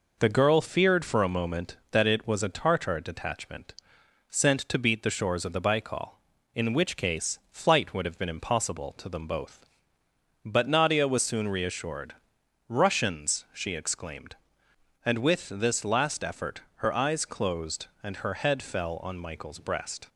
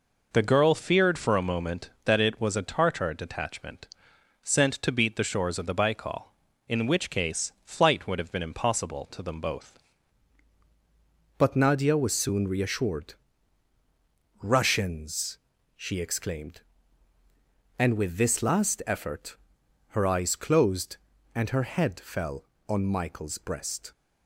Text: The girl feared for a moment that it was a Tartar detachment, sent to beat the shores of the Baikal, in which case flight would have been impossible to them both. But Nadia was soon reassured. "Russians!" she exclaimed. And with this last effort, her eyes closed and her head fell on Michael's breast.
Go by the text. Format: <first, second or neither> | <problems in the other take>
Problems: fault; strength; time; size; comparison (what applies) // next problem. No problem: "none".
first | changes voice at "But"; from 11.3 s on; 12.6 s long